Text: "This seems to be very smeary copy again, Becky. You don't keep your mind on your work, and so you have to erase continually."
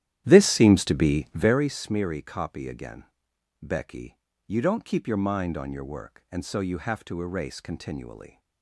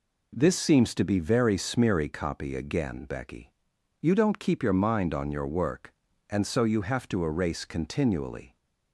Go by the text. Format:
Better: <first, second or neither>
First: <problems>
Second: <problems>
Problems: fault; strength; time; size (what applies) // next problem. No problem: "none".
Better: second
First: starts louder than the rest; strong; until 1.6 s; 11.5 dB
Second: none